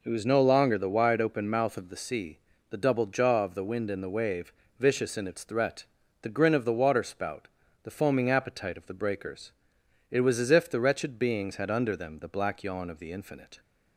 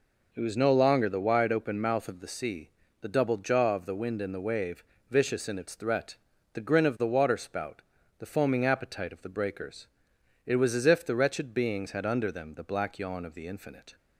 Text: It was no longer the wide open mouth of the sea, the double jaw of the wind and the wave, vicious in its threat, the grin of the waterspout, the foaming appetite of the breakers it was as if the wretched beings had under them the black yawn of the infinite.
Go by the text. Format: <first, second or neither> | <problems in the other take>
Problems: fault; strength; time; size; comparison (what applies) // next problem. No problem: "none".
neither | pauses between "breakers" and "it"; noticeable; the same in both